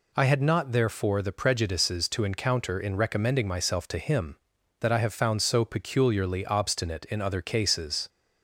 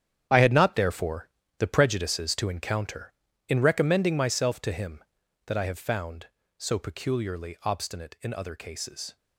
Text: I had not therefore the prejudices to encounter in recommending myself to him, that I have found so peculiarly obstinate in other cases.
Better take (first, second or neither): first